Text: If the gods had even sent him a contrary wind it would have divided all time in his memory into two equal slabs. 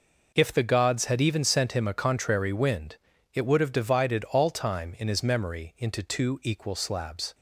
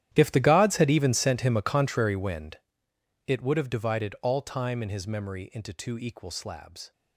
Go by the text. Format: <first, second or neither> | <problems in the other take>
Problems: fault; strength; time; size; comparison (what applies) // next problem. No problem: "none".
first | gets quieter; strong; throughout; 18.5 dB // pauses between "wind" and "it"; noticeable; at 2.5 s; 0.70 s long; also in the first